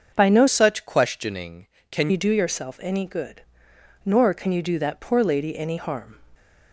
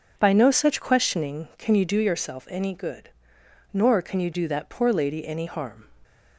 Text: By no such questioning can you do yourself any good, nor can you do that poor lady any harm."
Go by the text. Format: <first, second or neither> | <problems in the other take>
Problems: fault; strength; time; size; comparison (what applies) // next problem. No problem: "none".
second | starts louder than the rest; until 1.1 s; 6.5 dB // changes voice from "such" to "can"; from 0.4 to 2.0 s; 1.6 s long